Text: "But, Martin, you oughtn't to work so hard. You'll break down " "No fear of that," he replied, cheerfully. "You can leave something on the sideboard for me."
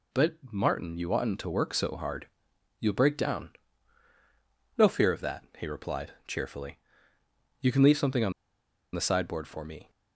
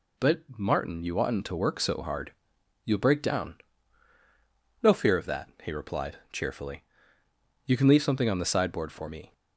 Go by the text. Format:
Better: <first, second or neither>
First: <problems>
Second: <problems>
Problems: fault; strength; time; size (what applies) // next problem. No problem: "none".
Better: second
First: pauses between "on" and "the"; noticeable; at 8.3 s; 0.61 s long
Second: none